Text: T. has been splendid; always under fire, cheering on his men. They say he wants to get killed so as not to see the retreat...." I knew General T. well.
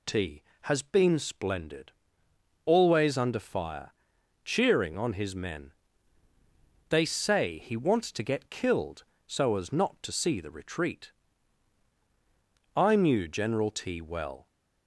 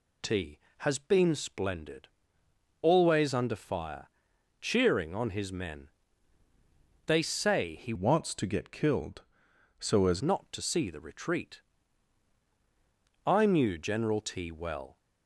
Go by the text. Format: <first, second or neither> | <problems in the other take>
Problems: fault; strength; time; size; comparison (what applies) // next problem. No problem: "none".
first | changes voice from "wants" to "as"; from 7.9 to 10.2 s; 2.3 s long